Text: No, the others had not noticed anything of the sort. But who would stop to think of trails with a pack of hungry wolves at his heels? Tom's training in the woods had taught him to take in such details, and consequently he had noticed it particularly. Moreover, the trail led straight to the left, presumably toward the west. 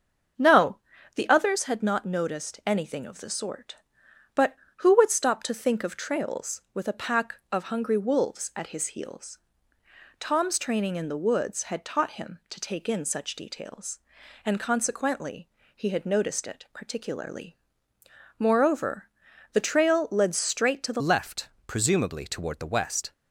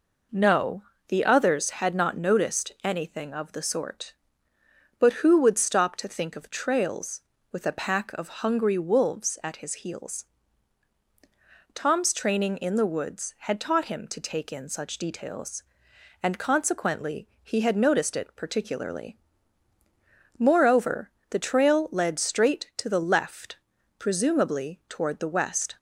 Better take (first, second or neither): second